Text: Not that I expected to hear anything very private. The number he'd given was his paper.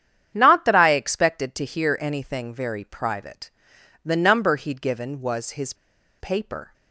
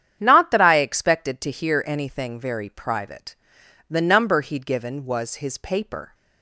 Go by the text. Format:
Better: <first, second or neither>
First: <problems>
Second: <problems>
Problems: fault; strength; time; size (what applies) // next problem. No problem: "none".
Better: second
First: starts louder than the rest; strong; until 1.3 s; 9 dB // pauses between "his" and "paper"; noticeable; at 5.7 s; 0.46 s long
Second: starts louder than the rest; strong; until 1.2 s; 9 dB